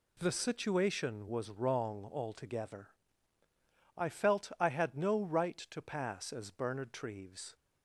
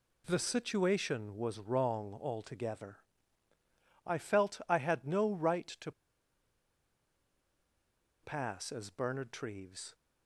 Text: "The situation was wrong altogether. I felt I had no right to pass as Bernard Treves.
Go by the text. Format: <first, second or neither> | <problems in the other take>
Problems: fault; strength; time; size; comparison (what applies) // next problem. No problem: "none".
first | pauses between "to" and "pass"; strong; at 5.9 s; 2.3 s long